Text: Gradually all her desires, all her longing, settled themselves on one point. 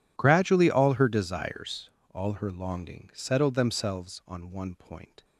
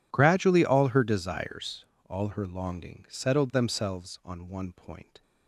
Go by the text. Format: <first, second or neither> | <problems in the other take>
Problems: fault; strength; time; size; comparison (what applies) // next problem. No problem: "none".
neither | none